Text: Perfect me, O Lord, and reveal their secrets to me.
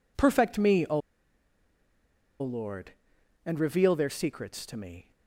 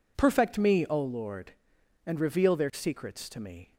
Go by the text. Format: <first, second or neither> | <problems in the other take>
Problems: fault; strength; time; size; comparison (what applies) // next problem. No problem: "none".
second | pauses between "O" and "Lord"; strong; at 0.9 s; 1.4 s long